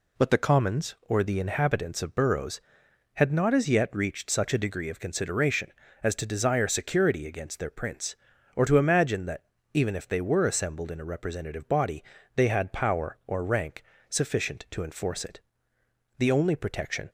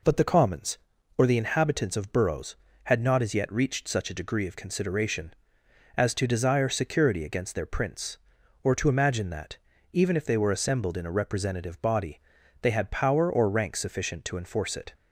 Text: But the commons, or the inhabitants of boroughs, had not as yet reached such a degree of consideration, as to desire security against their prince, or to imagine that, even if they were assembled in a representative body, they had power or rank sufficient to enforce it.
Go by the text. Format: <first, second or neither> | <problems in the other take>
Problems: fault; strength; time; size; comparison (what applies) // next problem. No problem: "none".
second | pauses between "rank" and "sufficient"; slight; at 13.8 s; 0.26 s long // goes on to say "The only protection"; noticeable; from 16.1 s on; 0.92 s long